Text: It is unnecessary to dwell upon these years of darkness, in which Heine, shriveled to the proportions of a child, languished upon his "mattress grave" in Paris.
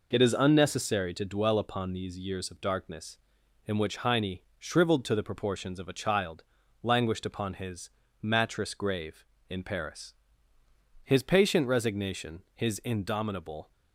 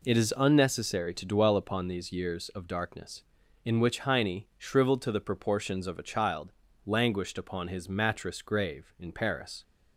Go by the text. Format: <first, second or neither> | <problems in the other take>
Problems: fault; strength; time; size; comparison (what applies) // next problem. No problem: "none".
second | pauses between "his" and "mattress"; slight; at 7.8 s; 0.32 s long // goes on to say "His patient resignation his indomitable"; strong; from 11.0 s on; 2.7 s long